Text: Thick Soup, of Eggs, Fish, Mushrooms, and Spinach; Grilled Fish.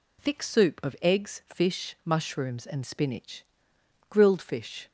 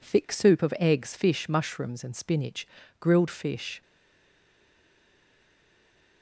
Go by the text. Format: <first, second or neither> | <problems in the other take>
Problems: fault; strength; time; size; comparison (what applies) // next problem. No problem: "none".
first | stays silent after the last word; from 3.8 s on; 2.4 s long